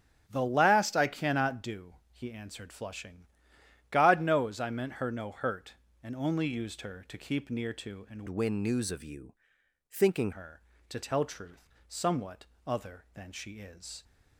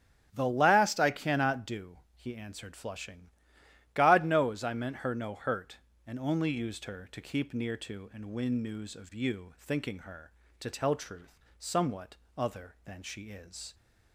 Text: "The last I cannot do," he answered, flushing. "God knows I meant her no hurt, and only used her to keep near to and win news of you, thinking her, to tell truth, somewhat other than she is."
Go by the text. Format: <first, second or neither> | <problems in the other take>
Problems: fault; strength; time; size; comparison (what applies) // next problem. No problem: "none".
second | starts louder than the rest; strong; until 1.2 s; 9 dB; strong in the second // changes voice from "win" to "thinking"; from 8.2 to 10.3 s; 2.1 s long // pauses between "somewhat" and "other"; slight; at 12.4 s; 0.22 s long; slight in the second